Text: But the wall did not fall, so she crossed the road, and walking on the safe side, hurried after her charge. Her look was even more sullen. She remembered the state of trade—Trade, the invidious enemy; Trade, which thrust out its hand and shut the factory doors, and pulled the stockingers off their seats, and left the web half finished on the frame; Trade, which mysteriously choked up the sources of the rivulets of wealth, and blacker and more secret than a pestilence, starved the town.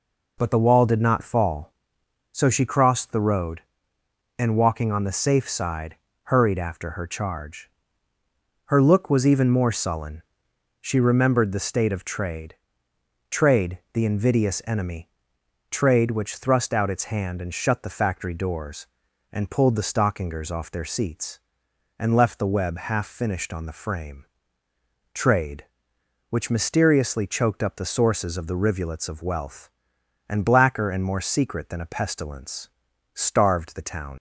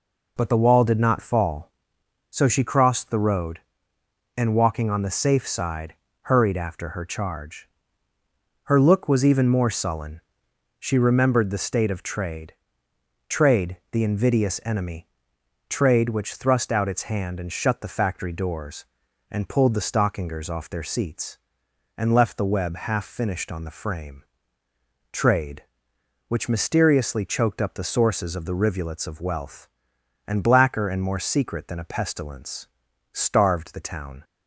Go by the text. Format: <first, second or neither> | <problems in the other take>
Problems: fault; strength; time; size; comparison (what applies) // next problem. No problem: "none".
second | leaves "town" unfinished; at 34.1 s; 70 ms